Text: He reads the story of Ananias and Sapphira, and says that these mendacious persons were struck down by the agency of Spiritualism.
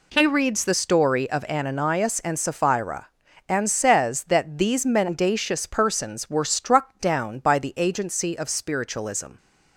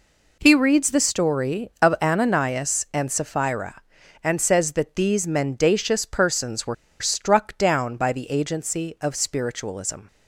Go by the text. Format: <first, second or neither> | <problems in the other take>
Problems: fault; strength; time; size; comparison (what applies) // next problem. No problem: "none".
first | pauses between "were" and "struck"; slight; at 6.7 s; 0.27 s long